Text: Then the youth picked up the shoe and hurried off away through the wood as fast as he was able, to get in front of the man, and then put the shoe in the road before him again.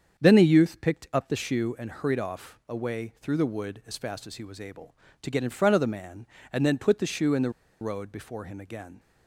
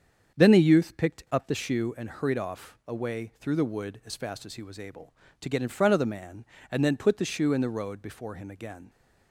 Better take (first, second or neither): second